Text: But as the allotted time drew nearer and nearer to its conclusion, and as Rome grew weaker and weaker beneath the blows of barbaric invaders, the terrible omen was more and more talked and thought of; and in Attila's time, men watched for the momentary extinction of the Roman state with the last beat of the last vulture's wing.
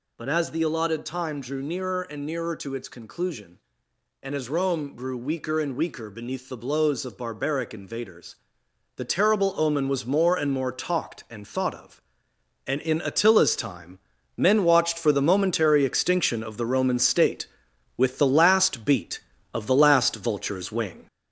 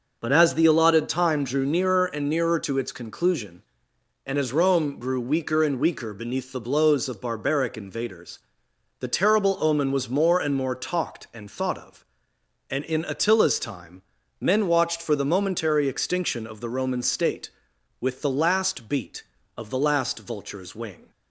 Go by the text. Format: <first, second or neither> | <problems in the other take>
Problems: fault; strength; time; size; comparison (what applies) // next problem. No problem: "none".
second | gets louder; noticeable; throughout; 4.5 dB